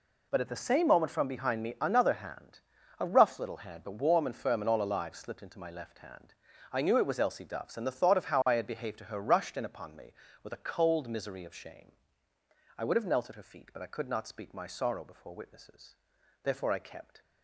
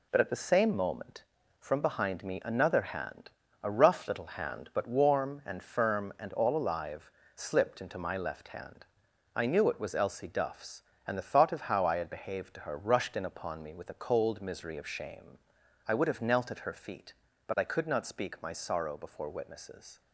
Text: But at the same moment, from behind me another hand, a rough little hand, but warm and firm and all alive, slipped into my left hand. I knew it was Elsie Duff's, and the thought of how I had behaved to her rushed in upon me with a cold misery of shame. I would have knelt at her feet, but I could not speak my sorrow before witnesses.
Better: second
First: goes on to say "Therefore I kept"; noticeable; from 16.4 s on; 0.78 s long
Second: none

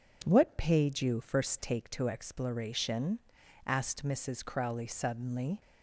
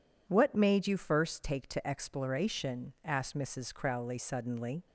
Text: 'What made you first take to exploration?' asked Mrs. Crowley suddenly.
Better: second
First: says "paid" for "made"; at 0.5 s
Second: none

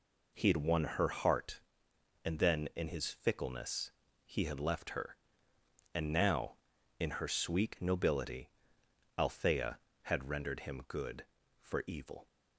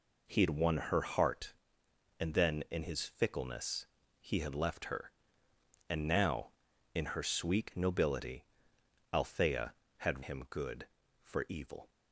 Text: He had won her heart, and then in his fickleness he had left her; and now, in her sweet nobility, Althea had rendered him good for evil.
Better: first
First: pauses between "fickleness" and "he"; slight; at 3.9 s; 0.34 s long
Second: pauses between "fickleness" and "he"; slight; at 3.8 s; 0.34 s long // skips "rendered"; at 10.2 s

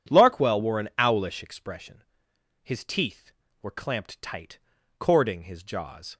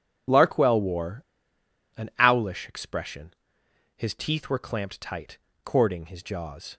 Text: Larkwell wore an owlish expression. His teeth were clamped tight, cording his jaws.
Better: first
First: none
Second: pauses between "wore" and "an"; noticeable; at 1.2 s; 0.73 s long

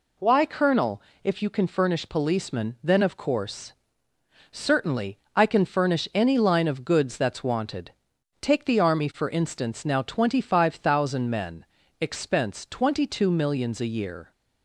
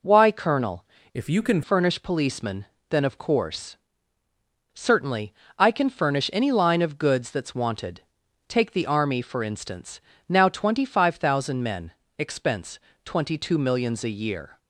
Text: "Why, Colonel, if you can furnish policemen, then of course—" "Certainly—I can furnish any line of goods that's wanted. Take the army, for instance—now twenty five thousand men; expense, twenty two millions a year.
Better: first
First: none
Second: changes voice from "if" to "can"; from 1.1 to 1.6 s; 0.5 s long

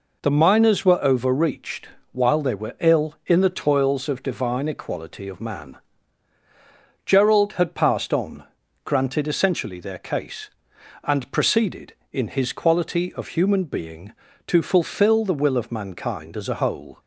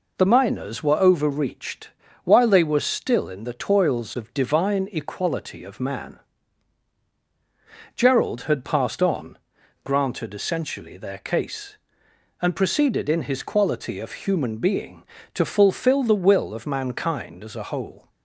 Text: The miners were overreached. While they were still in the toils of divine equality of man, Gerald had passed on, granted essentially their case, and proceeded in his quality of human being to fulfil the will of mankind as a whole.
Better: second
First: says "ill" for "still"; at 2.7 s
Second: none

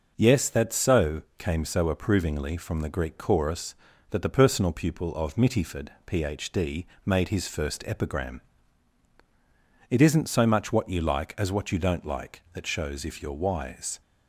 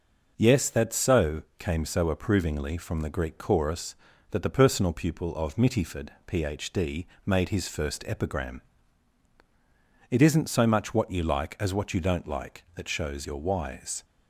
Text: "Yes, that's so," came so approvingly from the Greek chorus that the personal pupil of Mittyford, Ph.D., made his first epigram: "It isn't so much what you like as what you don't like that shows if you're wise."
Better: first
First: none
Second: skips "if"; at 13.2 s

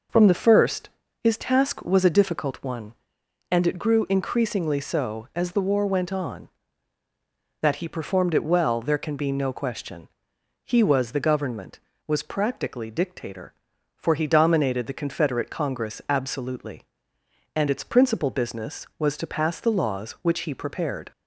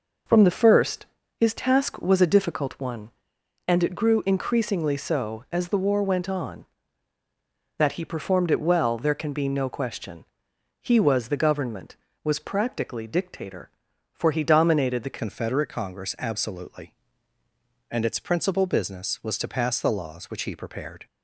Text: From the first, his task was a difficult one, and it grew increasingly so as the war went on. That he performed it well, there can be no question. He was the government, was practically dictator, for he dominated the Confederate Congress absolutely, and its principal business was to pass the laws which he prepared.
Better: first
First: none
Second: changes voice at "Confederate"; from 15.1 s on; 5.9 s long

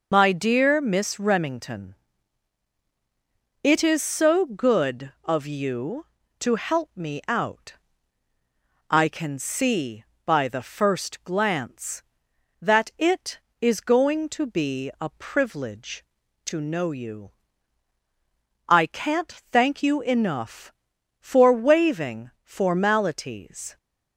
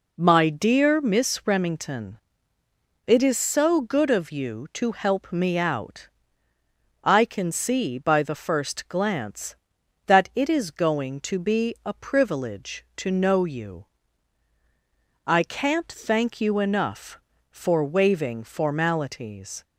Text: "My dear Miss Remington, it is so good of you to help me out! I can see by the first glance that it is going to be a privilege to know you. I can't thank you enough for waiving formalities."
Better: second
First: loses the start of "My"; at 0.1 s; 50 ms // pauses between "can't" and "thank"; slight; at 19.3 s; 0.22 s long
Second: none

